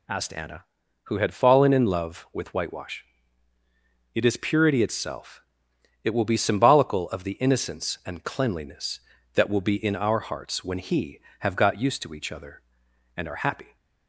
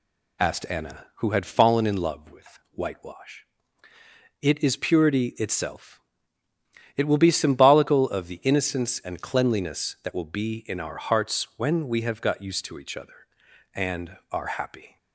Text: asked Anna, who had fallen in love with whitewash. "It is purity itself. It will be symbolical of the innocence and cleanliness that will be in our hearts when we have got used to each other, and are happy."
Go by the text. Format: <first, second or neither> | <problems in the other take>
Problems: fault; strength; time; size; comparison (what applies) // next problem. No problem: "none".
second | says "he" for "we"; at 10.7 s